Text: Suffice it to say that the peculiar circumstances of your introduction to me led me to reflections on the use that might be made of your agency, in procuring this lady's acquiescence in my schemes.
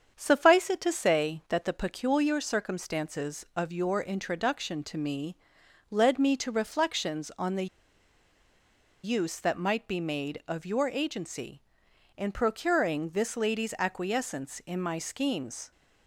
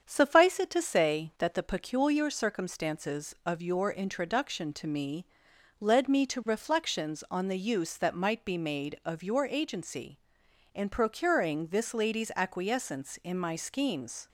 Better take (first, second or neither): second